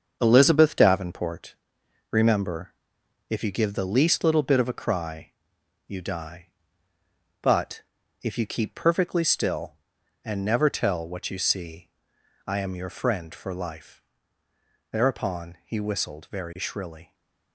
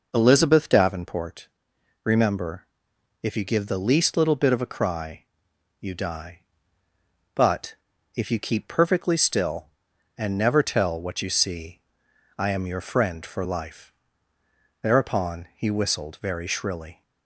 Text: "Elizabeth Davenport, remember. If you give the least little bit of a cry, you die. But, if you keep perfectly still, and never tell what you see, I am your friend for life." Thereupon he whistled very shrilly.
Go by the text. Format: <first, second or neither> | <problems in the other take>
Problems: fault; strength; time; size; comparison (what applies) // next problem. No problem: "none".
second | gets quieter; noticeable; throughout; 6 dB